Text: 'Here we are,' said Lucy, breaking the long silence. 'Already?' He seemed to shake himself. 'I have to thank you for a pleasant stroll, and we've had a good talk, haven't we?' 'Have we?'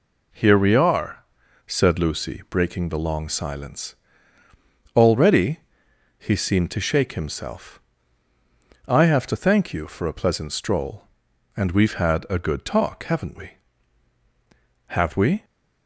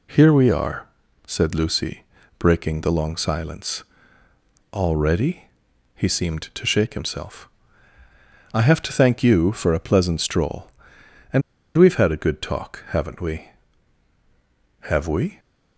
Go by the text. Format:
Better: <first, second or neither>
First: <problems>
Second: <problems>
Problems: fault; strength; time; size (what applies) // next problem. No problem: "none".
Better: first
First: none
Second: pauses between "and" and "we've"; slight; at 11.4 s; 0.35 s long